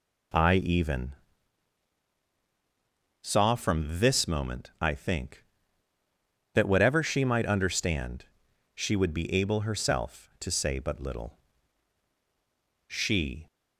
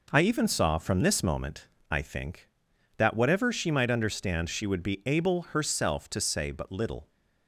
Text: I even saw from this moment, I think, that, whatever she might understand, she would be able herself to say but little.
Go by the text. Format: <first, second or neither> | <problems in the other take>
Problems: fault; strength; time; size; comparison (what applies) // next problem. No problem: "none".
second | pauses between "even" and "saw"; strong; at 1.1 s; 2.0 s long // goes on to say "She"; from 12.8 s on; 0.58 s long